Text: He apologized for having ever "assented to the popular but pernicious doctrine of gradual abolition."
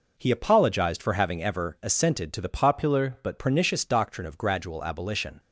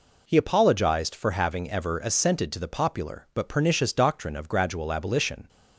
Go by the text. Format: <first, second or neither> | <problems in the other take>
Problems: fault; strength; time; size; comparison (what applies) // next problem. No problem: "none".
second | changes voice from "popular" to "but"; from 2.4 to 3.3 s; 0.9 s long